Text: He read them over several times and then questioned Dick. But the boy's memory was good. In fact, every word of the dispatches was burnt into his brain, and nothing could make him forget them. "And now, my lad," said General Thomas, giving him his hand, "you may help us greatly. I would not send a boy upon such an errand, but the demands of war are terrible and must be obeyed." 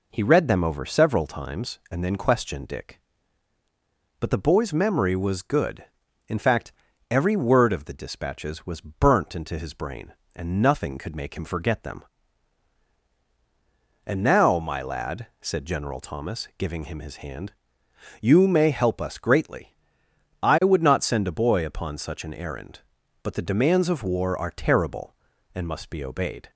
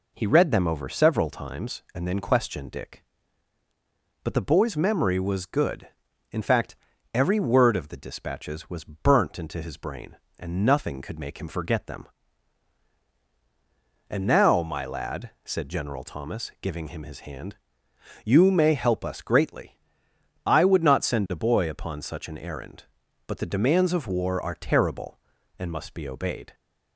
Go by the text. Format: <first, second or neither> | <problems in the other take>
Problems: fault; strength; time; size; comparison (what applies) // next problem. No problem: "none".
neither | none